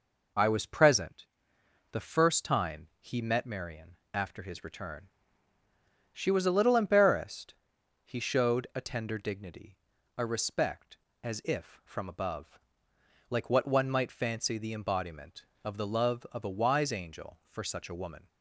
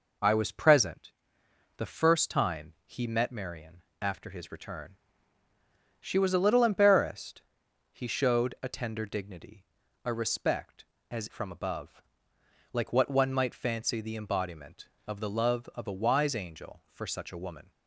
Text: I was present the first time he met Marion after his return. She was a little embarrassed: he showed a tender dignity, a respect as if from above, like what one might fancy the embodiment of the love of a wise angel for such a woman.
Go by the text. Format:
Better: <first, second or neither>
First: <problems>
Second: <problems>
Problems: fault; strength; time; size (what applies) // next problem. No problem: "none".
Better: first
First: pauses between "present" and "the"; noticeable; at 1.2 s; 0.64 s long // pauses between "Marion" and "after"; slight; at 3.9 s; 0.16 s long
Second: pauses between "present" and "the"; noticeable; at 1.1 s; 0.64 s long // pauses between "Marion" and "after"; slight; at 3.8 s; 0.18 s long // skips "if"; at 11.2 s